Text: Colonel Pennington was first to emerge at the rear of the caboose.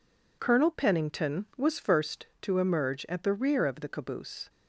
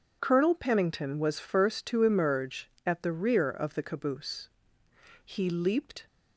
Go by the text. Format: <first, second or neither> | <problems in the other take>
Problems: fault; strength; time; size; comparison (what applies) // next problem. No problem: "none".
first | starts louder than the rest; noticeable; until 1.2 s; 6 dB // goes on to say "He leaped"; noticeable; from 5.2 s on; 0.82 s long